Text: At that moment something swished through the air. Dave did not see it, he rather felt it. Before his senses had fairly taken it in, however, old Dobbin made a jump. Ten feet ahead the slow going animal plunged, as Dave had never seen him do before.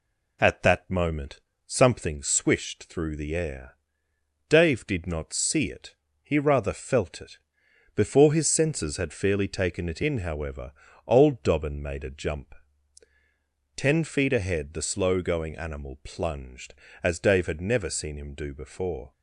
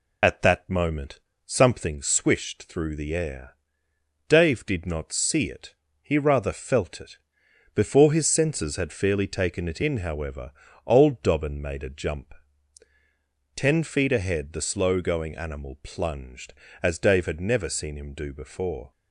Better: first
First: pauses between "moment" and "something"; slight; at 1.4 s; 0.24 s long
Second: loses the start of "At"; at 0.2 s; 40 ms // pauses between "moment" and "something"; slight; at 1.2 s; 0.24 s long

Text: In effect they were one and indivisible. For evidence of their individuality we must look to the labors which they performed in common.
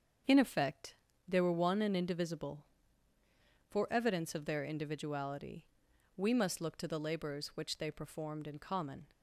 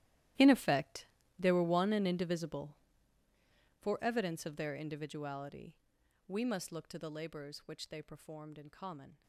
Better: first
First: starts louder than the rest; until 1.6 s; 7 dB // pauses between "effect" and "they"; slight; at 0.9 s; 0.34 s long // pauses between "individuality" and "we"; noticeable; at 5.6 s; 0.50 s long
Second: gets quieter; strong; throughout; 18 dB // starts louder than the rest; strong; until 1.7 s; 14 dB // pauses between "effect" and "they"; slight; at 1.0 s; 0.34 s long // pauses between "individuality" and "we"; noticeable; at 5.7 s; 0.50 s long

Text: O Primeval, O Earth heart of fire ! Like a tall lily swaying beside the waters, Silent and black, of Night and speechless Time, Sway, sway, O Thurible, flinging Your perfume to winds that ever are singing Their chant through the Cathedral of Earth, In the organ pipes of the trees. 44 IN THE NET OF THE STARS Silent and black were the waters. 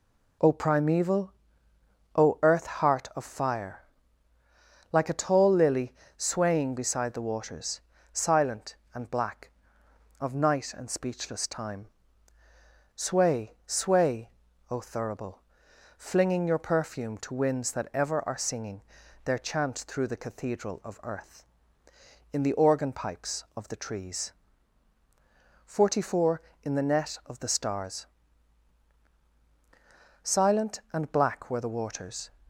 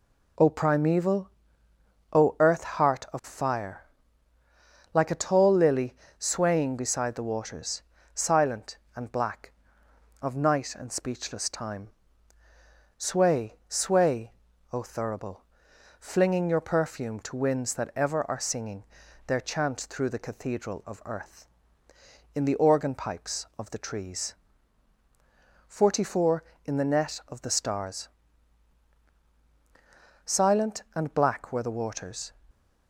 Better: neither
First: pauses between "lily" and "swaying"; slight; at 5.9 s; 0.24 s long // pauses between "singing" and "Their"; at 18.8 s; 0.40 s long // pauses between "STARS" and "Silent"; strong; at 28.0 s; 2.2 s long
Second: pauses between "lily" and "swaying"; slight; at 5.9 s; 0.24 s long // pauses between "singing" and "Their"; at 18.8 s; 0.40 s long // pauses between "STARS" and "Silent"; strong; at 28.0 s; 2.2 s long

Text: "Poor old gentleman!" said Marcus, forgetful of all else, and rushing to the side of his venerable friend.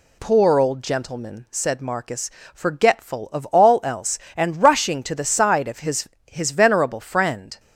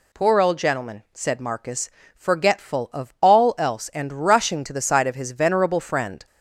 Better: second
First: says "his" twice; at 6.2 s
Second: none

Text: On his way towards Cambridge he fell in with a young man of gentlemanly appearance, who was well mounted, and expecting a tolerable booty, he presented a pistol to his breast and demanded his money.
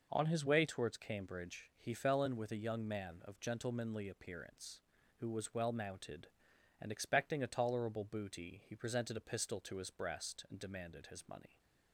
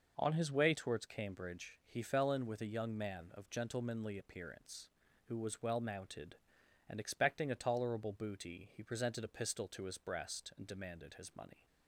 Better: neither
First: none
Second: none

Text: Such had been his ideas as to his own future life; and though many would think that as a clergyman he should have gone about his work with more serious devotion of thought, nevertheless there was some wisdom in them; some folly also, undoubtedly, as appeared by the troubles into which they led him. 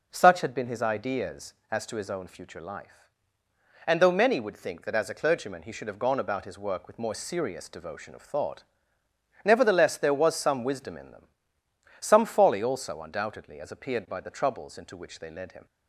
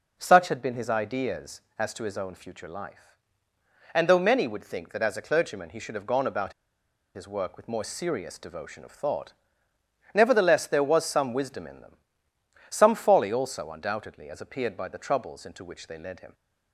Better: first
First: none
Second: pauses between "about" and "his"; noticeable; at 6.5 s; 0.62 s long

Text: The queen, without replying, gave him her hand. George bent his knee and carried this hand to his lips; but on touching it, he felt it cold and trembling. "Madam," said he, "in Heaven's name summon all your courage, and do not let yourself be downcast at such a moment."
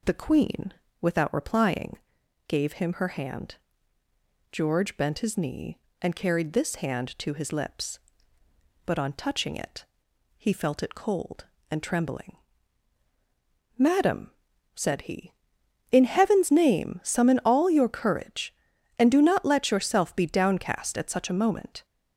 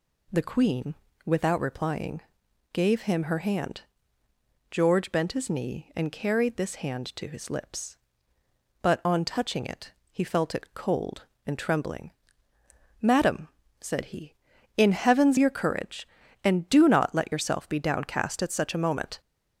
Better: first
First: none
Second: skips "name summon all"; at 15.3 s

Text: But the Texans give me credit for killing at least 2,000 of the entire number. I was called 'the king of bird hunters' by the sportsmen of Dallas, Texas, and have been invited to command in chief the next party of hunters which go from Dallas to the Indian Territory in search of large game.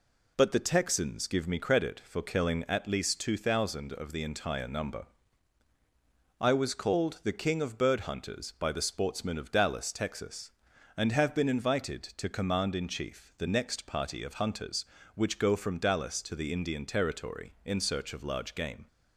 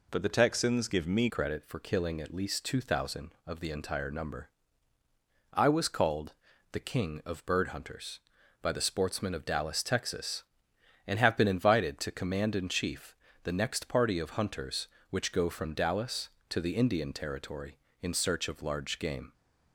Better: first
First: none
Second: changes voice at "credit"; from 1.2 s on; 18.1 s long // pauses between "called" and "the"; at 6.3 s; 0.38 s long // pauses between "chief" and "the"; slight; at 13.1 s; 0.28 s long

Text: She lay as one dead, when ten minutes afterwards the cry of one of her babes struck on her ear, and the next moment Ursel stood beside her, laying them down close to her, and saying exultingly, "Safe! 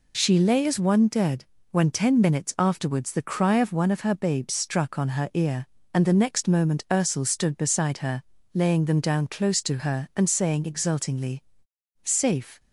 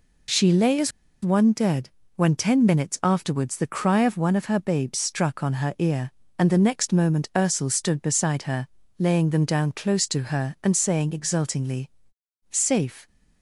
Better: first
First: none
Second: pauses between "as" and "one"; slight; at 0.9 s; 0.33 s long

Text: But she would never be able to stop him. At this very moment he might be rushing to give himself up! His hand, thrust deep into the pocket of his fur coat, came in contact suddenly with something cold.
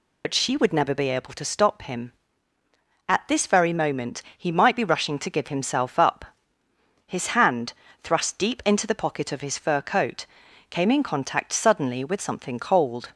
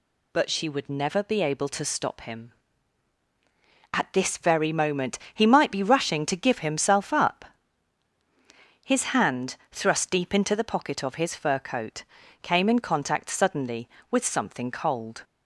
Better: second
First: loses the start of "But"; at 0.2 s; 60 ms // pauses between "moment" and "he"; slight; at 4.2 s; 0.16 s long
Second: pauses between "moment" and "he"; slight; at 5.1 s; 0.16 s long

